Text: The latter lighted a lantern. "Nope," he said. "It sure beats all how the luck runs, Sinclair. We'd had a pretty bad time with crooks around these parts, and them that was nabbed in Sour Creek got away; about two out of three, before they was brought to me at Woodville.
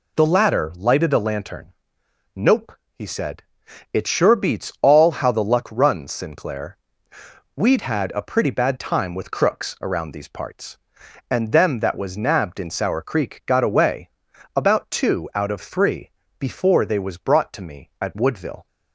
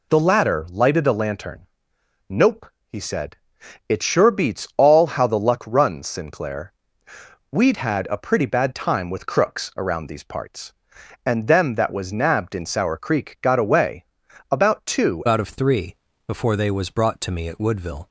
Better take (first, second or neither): first